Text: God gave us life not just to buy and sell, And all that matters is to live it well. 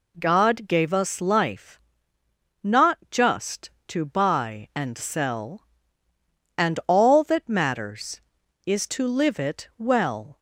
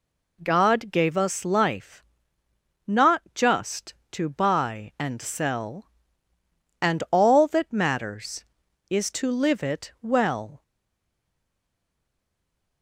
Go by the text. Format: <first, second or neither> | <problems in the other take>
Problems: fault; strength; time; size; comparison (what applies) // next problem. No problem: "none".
first | pauses between "life" and "not"; noticeable; at 2.0 s; 0.84 s long; noticeable in the first // stays silent after the last word; from 10.6 s on; 2.2 s long